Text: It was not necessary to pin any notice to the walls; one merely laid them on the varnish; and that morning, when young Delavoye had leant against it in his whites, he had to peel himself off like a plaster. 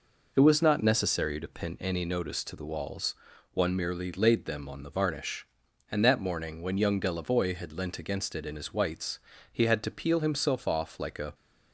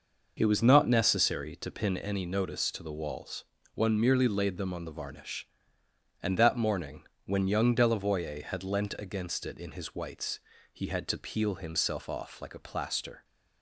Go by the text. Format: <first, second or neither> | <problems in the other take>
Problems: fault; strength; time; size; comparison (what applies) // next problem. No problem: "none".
second | stops before "plaster"; at 11.3 s